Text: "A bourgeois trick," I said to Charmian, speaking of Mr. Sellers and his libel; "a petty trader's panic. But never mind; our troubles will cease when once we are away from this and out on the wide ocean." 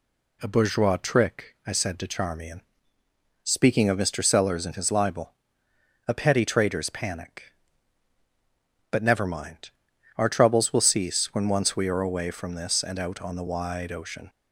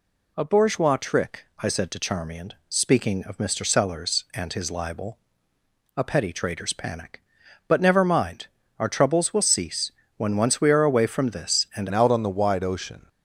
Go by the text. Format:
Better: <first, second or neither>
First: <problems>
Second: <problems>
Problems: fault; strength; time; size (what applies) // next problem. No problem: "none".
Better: first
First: none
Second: pauses between "cease" and "when"; slight; at 9.9 s; 0.24 s long // changes voice at "out"; from 11.9 s on; 1.1 s long